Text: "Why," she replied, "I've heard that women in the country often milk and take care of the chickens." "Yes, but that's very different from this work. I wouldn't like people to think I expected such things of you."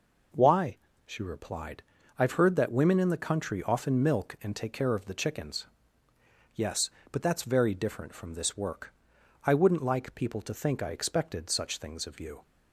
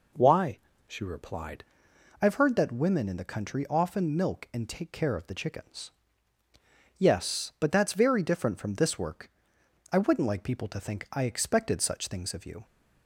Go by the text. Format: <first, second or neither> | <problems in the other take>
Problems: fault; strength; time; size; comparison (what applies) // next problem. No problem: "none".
first | changes voice at "I've"; from 2.2 s on; 10.4 s long